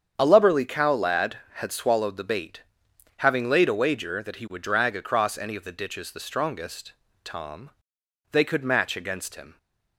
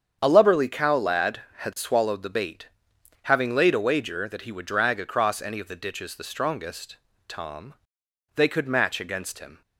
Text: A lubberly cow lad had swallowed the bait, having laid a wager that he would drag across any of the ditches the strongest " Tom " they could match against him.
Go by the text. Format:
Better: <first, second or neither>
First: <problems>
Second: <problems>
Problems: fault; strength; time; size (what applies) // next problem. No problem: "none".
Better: neither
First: starts louder than the rest; strong; until 1.1 s; 8 dB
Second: starts louder than the rest; strong; until 1.2 s; 8 dB